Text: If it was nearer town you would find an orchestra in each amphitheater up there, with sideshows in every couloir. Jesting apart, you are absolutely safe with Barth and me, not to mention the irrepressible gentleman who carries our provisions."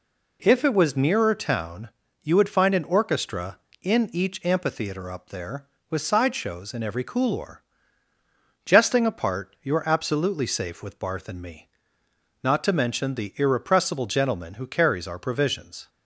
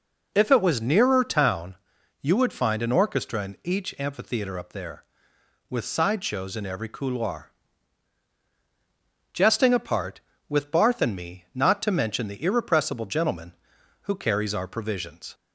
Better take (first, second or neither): first